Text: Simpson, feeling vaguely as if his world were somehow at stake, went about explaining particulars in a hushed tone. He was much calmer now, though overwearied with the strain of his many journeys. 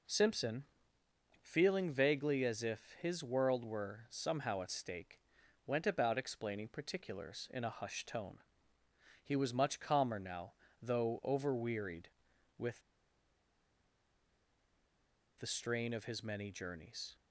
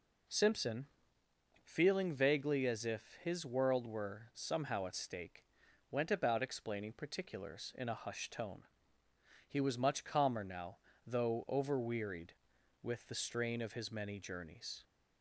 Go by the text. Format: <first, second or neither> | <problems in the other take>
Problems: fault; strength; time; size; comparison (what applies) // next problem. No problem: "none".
second | pauses between "with" and "the"; strong; at 12.8 s; 2.5 s long